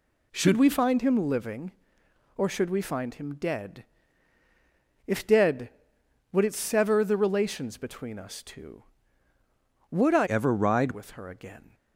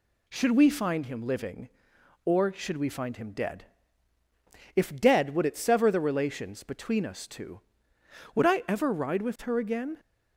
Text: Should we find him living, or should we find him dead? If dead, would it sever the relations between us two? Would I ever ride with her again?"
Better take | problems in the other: second | changes voice from "ever" to "ride"; from 10.2 to 10.9 s; 0.7 s long

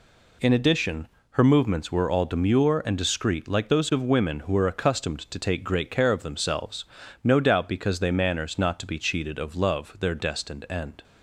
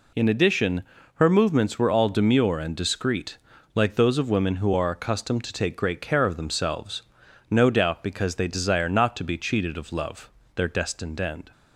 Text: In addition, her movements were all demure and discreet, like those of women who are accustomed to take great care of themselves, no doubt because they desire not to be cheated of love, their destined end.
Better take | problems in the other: second | says "manners" for "desire"; at 8.1 s

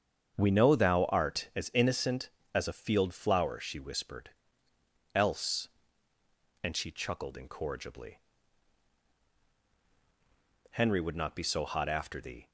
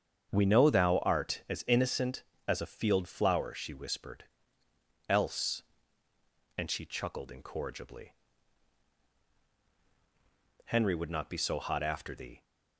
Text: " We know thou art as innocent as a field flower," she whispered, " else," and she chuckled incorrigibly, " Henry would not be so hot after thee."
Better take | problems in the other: neither | starts louder than the rest; strong; the same in both

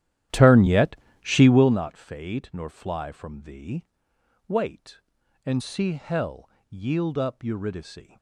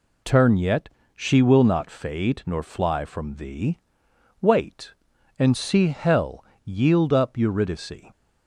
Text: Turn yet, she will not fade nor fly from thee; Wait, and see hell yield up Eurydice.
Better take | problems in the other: second | starts louder than the rest; strong; until 1.8 s; 12 dB // pauses between "hell" and "yield"; slight; at 6.4 s; 0.20 s long; slight in the second

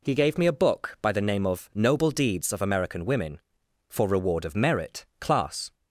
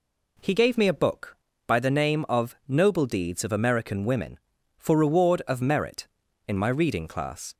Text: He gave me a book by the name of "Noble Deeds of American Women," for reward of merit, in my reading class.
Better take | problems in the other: second | skips "in my reading"; at 5.1 s

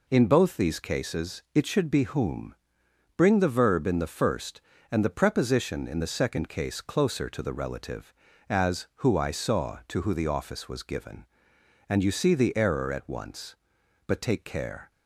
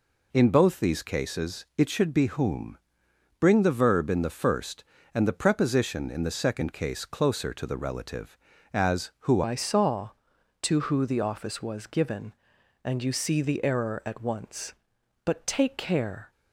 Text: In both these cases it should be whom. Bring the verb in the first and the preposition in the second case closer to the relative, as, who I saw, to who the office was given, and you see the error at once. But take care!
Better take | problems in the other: first | changes voice at "I"; from 9.4 s on; 6.9 s long

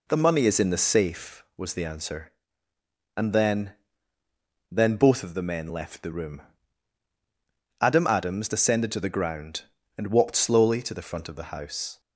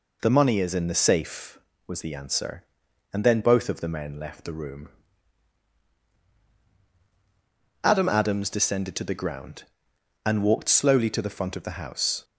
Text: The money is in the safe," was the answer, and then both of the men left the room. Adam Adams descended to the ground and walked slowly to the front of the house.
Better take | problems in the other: second | says "then" twice; at 4.7 s

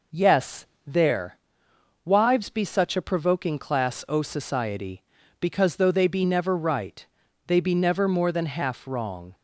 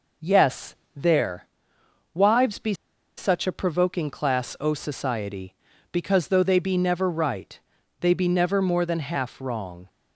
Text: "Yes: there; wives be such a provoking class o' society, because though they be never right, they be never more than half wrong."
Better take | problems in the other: first | pauses between "be" and "such"; at 2.7 s; 0.42 s long

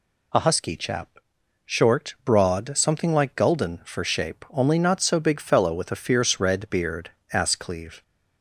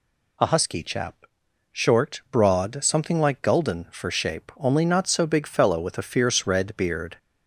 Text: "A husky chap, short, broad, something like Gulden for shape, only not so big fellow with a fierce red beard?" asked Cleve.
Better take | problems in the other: first | stops before "asked Cleve"; at 7.1 s

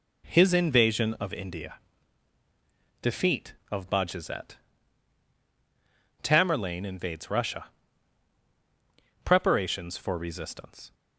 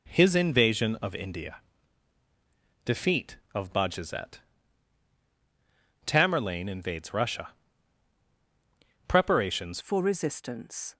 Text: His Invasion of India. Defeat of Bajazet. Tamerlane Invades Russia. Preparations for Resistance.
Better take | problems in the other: first | changes voice at "for"; from 9.7 s on; 1.2 s long

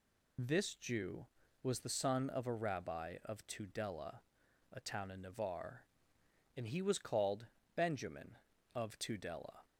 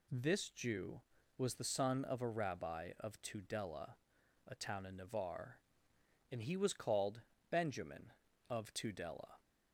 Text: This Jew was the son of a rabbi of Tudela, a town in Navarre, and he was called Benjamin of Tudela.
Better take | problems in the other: second | loses the start of "This"; at 0.3 s; 45 ms // pauses between "called" and "Benjamin"; slight; at 7.4 s; 0.30 s long; slight in the second

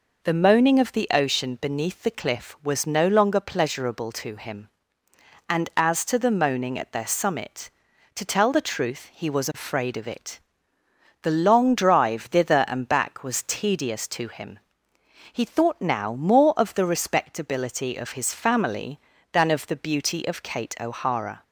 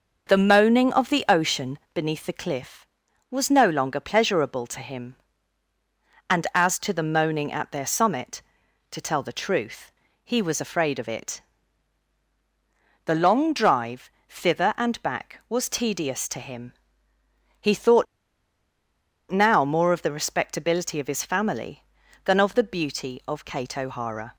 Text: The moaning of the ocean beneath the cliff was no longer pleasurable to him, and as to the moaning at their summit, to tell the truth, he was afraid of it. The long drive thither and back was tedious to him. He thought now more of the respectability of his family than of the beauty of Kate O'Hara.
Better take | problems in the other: first | starts louder than the rest; noticeable; until 1.3 s; 6 dB // pauses between "ocean" and "beneath"; slight; at 1.7 s; 0.16 s long // pauses between "drive" and "thither"; slight; at 14.0 s; 0.18 s long // pauses between "thought" and "now"; strong; at 18.0 s; 1.2 s long

